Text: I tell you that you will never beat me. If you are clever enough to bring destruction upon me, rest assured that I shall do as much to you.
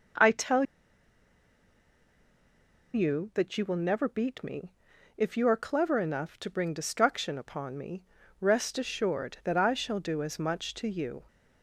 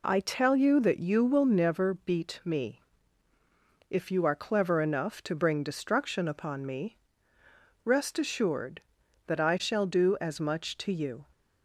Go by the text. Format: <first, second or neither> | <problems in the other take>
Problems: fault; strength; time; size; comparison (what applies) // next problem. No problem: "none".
second | pauses between "tell" and "you"; strong; at 0.6 s; 2.2 s long